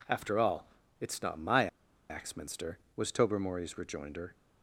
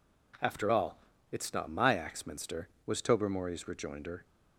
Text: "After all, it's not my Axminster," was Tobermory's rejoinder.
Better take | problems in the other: second | pauses between "my" and "Axminster"; at 1.6 s; 0.42 s long

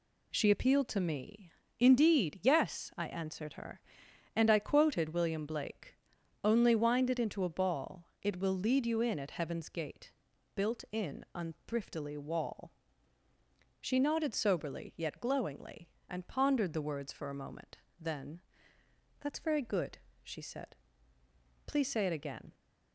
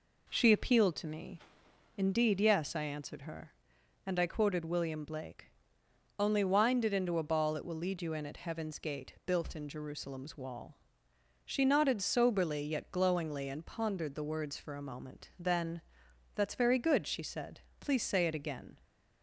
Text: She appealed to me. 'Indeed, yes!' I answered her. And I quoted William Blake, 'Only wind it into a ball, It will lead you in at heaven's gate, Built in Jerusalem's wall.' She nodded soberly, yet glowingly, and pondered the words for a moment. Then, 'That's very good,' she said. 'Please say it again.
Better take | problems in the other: second | says "Unthriftily" for "Jerusalem's"; at 11.3 s

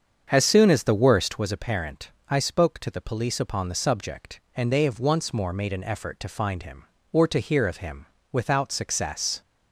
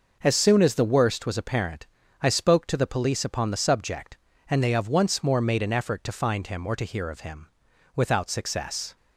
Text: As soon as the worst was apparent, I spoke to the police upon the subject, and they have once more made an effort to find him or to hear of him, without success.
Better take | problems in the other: second | starts louder than the rest; strong; until 1.5 s; 7.5 dB

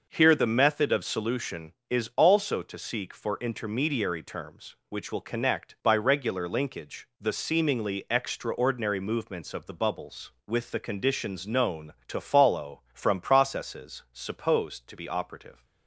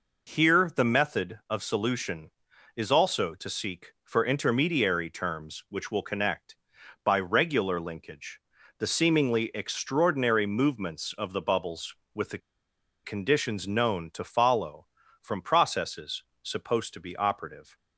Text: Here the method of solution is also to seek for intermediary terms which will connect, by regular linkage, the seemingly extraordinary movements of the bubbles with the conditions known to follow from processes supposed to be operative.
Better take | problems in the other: first | pauses between "the" and "conditions"; noticeable; at 12.3 s; 0.66 s long // pauses between "processes" and "supposed"; slight; at 16.2 s; 0.20 s long

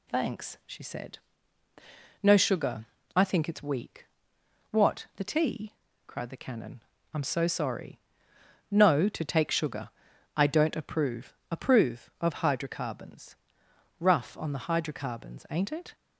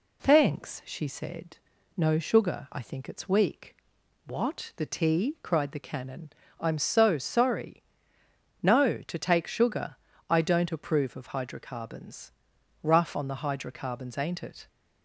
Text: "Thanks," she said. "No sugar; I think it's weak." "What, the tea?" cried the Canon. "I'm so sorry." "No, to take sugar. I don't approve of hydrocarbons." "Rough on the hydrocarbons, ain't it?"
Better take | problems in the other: second | says "approve" twice; at 11.5 s

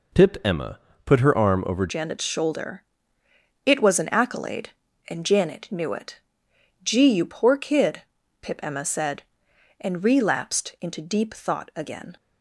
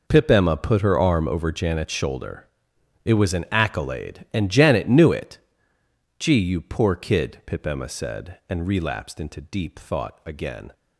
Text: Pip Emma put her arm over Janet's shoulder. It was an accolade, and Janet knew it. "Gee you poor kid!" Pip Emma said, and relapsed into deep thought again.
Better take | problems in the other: second | pauses between "Emma" and "put"; slight; at 0.7 s; 0.26 s long // changes voice at "Janet's"; from 1.8 s on; 10.3 s long

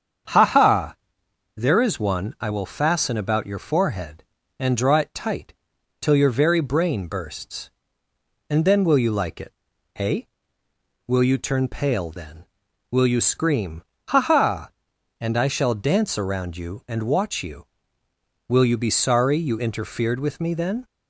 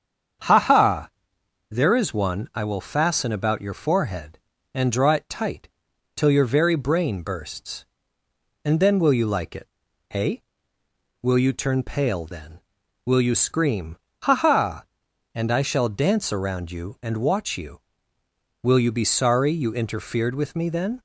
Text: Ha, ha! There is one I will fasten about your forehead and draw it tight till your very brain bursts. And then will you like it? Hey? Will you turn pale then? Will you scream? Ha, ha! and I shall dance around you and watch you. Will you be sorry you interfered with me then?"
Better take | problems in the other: neither | starts louder than the rest; strong; the same in both // pauses between "tight" and "till"; noticeable; the same in both

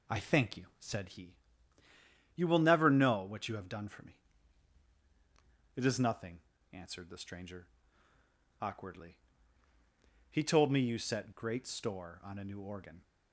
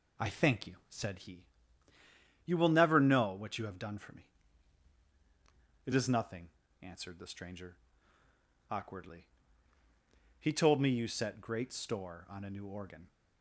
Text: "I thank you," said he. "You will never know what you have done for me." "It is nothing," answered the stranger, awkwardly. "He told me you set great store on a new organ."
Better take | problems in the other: neither | none

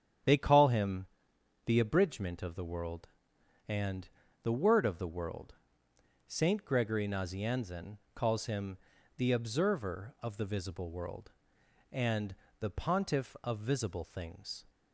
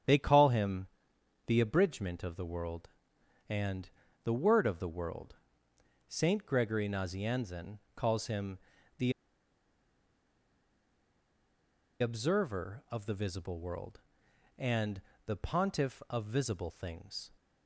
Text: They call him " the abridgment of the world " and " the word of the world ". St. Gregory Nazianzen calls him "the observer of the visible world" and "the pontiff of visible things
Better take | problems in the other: first | starts louder than the rest; strong; until 1.3 s; 7.5 dB; strong in the first // pauses between "Nazianzen" and "calls"; slight; at 7.7 s; 0.16 s long; slight in the first // pauses between "him" and "the"; at 8.5 s; 0.40 s long; also in the first // pauses between "the" and "observer"; strong; at 9.1 s; 2.8 s long // pauses between "and" and "the"; slight; at 15.0 s; 0.24 s long; slight in the first

